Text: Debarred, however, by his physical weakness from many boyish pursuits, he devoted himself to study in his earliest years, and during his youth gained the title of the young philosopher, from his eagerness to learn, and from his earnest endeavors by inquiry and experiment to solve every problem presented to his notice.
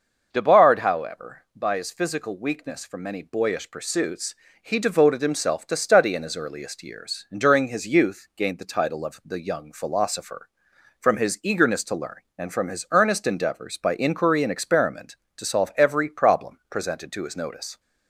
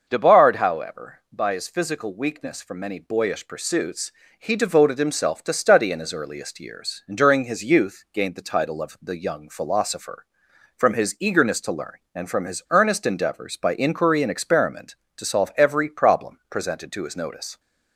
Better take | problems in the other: neither | starts louder than the rest; noticeable; the same in both

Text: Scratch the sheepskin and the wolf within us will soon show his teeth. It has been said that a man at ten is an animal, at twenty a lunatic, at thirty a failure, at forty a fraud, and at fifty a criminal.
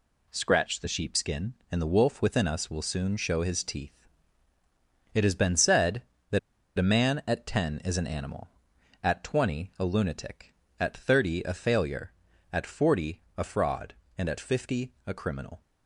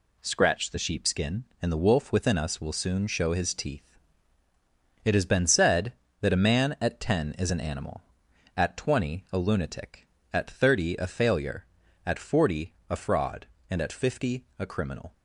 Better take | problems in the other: second | pauses between "that" and "a"; at 6.3 s; 0.38 s long // pauses between "forty" and "a"; slight; at 13.2 s; 0.16 s long; slight in the second

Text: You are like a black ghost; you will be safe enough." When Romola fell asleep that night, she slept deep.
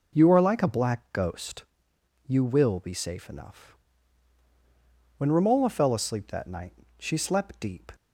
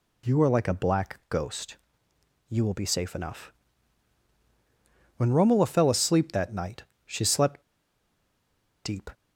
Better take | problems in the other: first | pauses between "slept" and "deep"; at 7.6 s; 1.2 s long

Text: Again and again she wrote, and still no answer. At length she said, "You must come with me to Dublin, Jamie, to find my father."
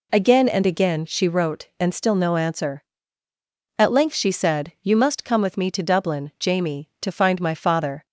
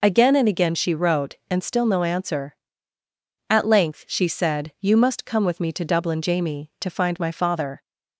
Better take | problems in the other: neither | none

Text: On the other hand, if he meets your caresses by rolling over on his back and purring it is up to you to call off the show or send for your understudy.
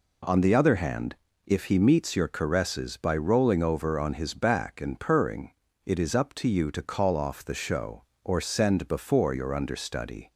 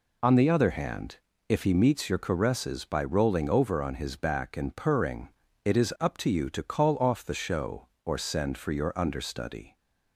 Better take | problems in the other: second | pauses between "purring" and "it"; slight; at 5.5 s; 0.34 s long; slight in the second // says "before" for "for"; at 8.8 s

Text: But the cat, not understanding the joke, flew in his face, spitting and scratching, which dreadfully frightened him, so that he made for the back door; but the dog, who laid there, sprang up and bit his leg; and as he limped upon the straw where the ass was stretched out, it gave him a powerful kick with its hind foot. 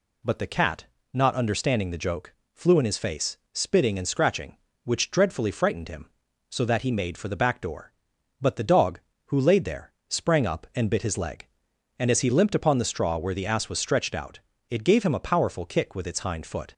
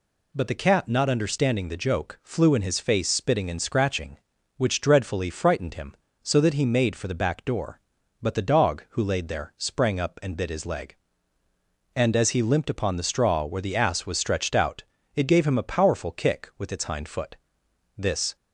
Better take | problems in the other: first | goes on to say "This"; slight; from 17.9 s on; 0.38 s long

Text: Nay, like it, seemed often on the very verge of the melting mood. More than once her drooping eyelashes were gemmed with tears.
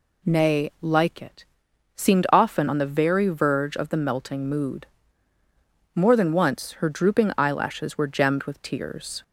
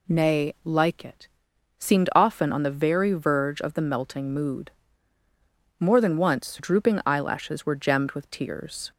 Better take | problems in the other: first | skips "her"; at 6.5 s

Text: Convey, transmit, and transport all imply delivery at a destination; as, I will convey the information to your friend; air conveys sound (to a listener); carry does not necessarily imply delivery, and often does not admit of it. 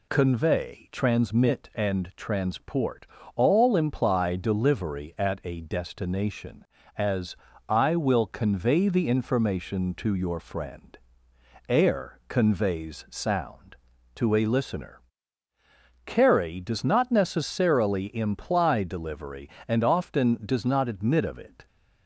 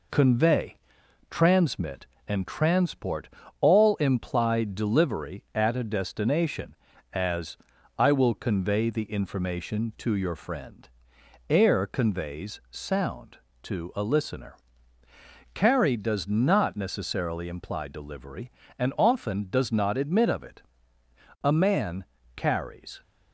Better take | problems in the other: first | pauses between "transport" and "all"; slight; at 3.2 s; 0.32 s long; slight in the first // goes on to say "A man carries"; from 21.4 s on; 1.6 s long

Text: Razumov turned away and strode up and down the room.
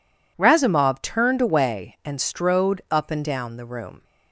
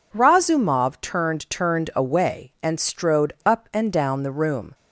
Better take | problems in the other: first | says "turned" twice; at 1.4 s

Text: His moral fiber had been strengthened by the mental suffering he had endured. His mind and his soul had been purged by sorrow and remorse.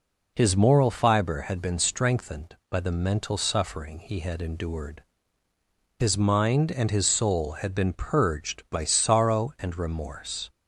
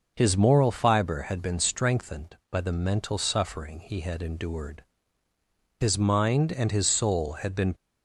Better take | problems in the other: first | stops before "purged by sorrow and remorse"; at 7.7 s

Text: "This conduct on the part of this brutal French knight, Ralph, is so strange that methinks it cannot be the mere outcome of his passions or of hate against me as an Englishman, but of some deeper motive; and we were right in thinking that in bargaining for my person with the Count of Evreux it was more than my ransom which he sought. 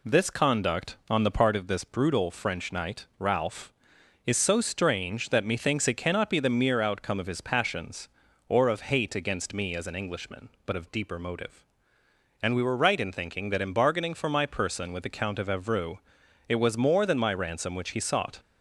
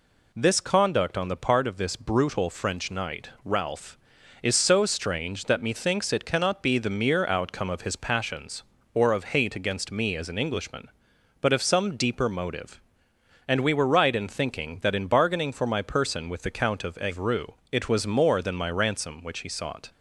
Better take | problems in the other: second | skips "some"; at 10.9 s // pauses between "Evreux" and "it"; noticeable; at 15.9 s; 0.48 s long; slight in the second

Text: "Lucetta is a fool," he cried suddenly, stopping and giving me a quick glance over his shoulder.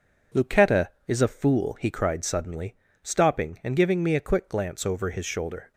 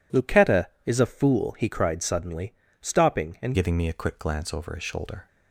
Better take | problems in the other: first | changes voice at "giving"; from 3.5 s on; 1.7 s long

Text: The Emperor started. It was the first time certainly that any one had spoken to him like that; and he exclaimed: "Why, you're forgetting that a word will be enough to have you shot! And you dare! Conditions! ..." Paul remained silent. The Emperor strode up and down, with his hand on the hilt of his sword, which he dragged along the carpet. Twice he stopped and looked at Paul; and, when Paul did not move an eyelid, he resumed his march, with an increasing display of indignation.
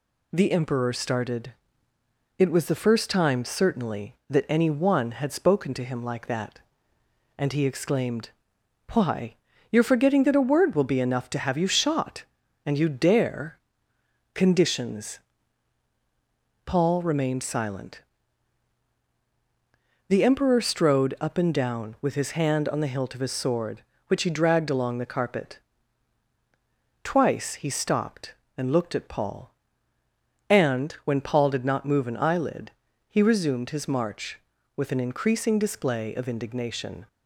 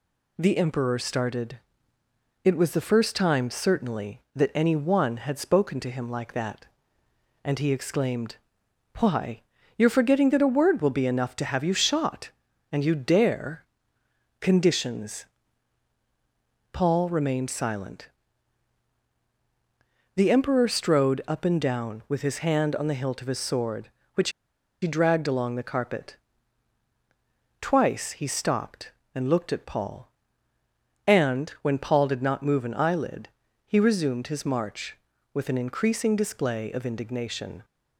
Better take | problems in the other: first | pauses between "which" and "he"; noticeable; at 24.3 s; 0.51 s long

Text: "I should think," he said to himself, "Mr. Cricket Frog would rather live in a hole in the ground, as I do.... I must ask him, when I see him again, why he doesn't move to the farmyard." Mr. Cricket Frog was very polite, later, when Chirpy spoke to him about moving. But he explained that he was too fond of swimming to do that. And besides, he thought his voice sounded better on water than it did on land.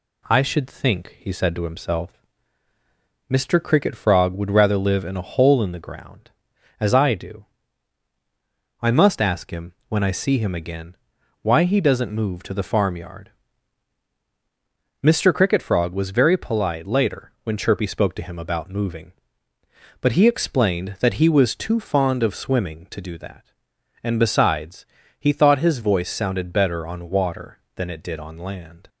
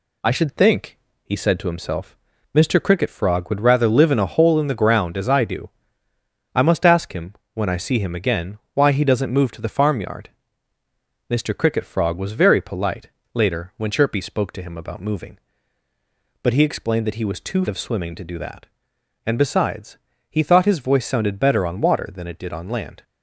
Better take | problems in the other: first | skips "fond"; at 17.6 s

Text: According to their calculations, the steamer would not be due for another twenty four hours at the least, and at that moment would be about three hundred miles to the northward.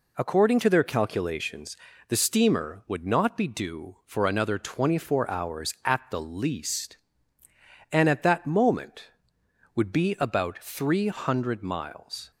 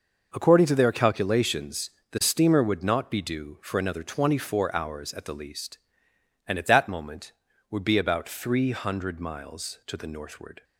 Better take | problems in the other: second | stops before "to the northward"; at 12.3 s

